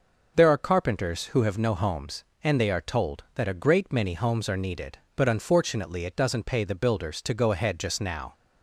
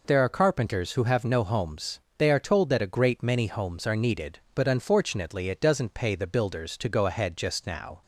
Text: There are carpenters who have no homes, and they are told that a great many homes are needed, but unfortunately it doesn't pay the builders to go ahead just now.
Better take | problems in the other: first | skips "and"; at 2.0 s

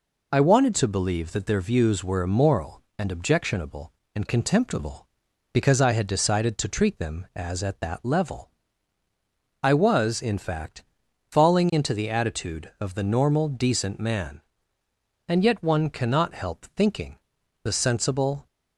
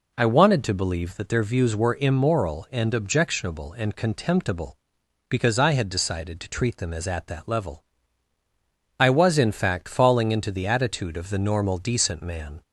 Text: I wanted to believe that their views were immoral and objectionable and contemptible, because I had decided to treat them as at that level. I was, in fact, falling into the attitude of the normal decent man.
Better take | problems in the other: second | goes on to say "And yet one cannot help thinking The sensible"; strong; from 15.2 s on; 3.1 s long

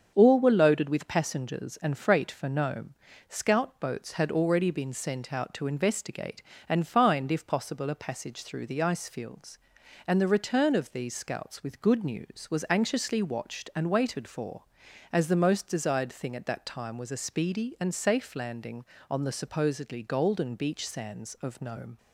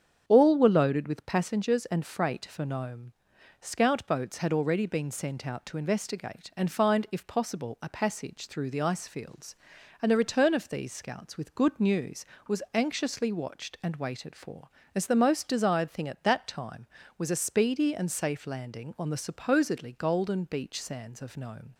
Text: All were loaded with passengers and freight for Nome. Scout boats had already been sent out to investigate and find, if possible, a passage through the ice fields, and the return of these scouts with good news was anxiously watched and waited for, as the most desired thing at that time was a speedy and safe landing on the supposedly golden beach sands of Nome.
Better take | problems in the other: neither | starts louder than the rest; the same in both

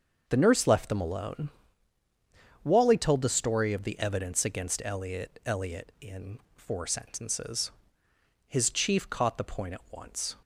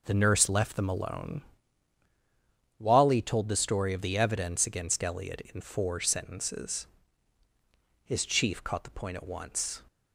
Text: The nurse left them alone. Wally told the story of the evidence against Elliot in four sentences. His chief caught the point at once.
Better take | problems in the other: second | starts louder than the rest; until 1.2 s; 6.5 dB // says "Elliot" twice; at 5.4 s // pauses between "in" and "four"; slight; at 6.3 s; 0.18 s long

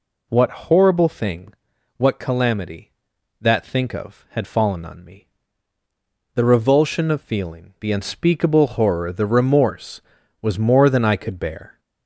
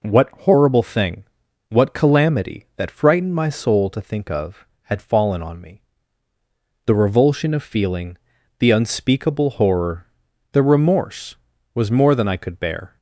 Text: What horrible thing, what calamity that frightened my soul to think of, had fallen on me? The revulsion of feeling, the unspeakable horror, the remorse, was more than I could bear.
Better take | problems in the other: second | skips "frightened my soul to"; at 3.6 s

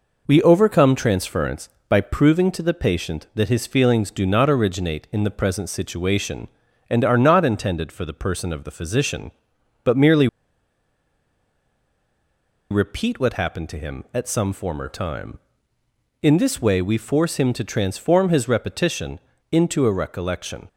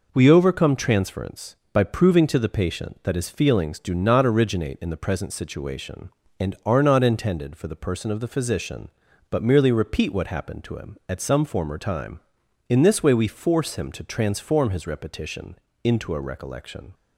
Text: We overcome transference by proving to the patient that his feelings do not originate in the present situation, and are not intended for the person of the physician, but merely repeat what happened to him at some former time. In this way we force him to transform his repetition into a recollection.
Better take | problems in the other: second | pauses between "merely" and "repeat"; strong; at 10.2 s; 2.4 s long // pauses between "repetition" and "into"; slight; at 19.2 s; 0.32 s long; slight in the second

